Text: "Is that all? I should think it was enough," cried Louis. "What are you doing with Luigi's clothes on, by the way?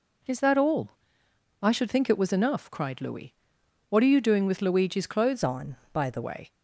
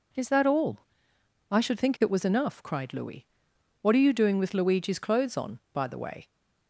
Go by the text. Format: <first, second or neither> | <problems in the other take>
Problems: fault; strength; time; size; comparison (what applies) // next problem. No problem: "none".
second | changes voice from "on" to "the"; from 5.4 to 6.2 s; 0.8 s long